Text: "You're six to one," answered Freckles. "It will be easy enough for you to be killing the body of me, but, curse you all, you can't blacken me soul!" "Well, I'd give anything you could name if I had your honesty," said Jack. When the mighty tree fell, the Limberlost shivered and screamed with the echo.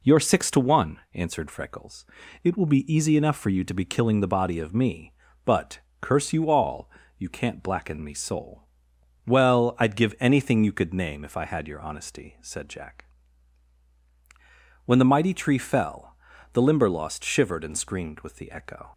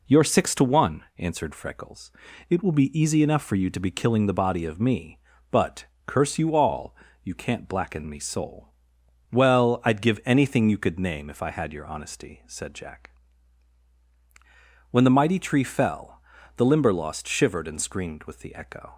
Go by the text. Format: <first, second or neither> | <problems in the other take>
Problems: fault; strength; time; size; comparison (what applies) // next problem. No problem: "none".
neither | none